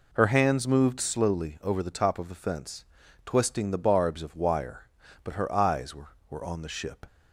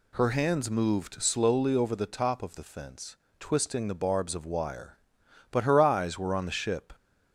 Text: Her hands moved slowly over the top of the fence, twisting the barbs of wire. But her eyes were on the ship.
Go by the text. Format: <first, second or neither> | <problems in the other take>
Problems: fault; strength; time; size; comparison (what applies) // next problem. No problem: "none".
second | says "were" twice; at 6.2 s